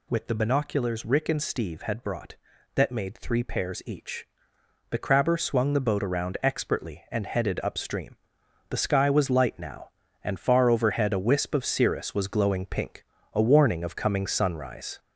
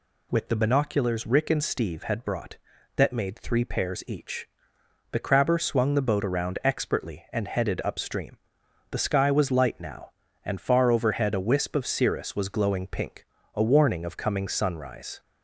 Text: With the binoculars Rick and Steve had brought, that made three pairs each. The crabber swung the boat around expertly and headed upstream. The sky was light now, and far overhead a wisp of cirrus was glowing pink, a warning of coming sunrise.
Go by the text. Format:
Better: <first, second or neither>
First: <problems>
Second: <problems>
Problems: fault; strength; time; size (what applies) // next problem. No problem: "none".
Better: second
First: gets louder; noticeable; throughout; 4.5 dB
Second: none